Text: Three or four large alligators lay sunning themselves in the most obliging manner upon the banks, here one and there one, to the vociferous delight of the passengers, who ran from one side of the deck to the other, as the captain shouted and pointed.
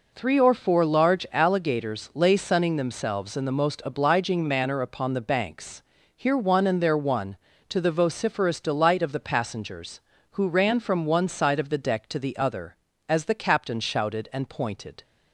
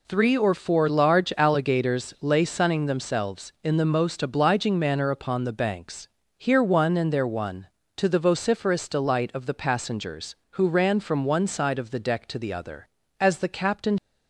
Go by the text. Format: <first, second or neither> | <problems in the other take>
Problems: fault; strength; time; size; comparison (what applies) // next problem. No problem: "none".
first | stops before "shouted and pointed"; at 13.9 s